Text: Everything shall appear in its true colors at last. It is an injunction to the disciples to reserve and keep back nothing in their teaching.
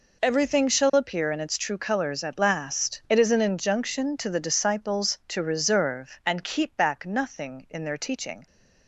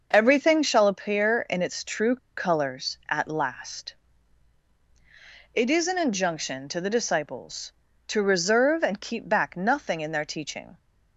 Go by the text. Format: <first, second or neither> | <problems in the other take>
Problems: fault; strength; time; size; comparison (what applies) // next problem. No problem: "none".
first | pauses between "true" and "colors"; slight; at 2.1 s; 0.19 s long